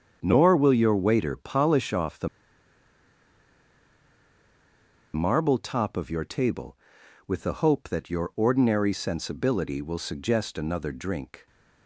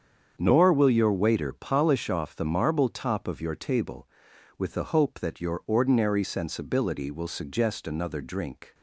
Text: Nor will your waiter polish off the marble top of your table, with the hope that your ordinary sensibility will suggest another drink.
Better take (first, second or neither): second